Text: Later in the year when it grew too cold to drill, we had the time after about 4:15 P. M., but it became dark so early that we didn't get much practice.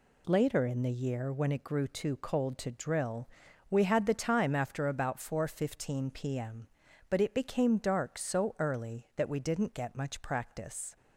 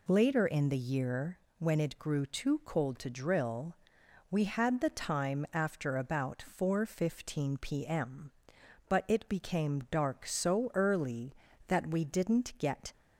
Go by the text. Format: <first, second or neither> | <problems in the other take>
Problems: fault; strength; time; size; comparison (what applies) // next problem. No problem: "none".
first | pauses between "year" and "when"; slight; at 1.3 s; 0.20 s long // stops before "much practice"; at 12.9 s